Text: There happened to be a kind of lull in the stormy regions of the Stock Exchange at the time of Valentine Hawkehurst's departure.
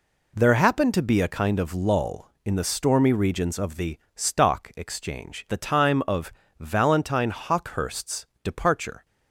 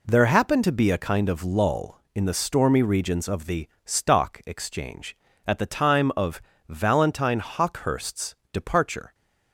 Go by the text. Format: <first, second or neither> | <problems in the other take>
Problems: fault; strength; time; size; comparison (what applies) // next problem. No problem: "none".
second | pauses between "the" and "Stock"; slight; at 3.9 s; 0.18 s long; slight in the second // skips "at"; at 5.4 s // pauses between "of" and "Valentine"; slight; at 6.3 s; 0.26 s long; slight in the second // pauses between "Hawkehurst's" and "departure"; slight; at 8.2 s; 0.16 s long; slight in the second